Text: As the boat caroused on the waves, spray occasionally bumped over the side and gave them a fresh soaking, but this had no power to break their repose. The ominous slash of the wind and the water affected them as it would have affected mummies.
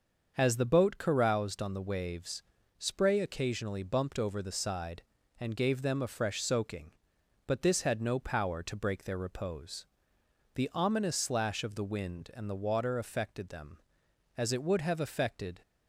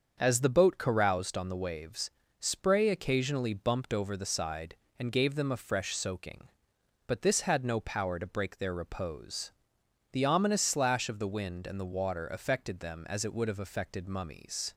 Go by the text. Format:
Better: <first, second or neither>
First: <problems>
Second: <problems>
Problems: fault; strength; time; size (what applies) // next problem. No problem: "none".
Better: second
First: starts louder than the rest; until 1.4 s; 6.5 dB // stops before "mummies"; at 15.6 s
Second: starts louder than the rest; until 1.2 s; 7 dB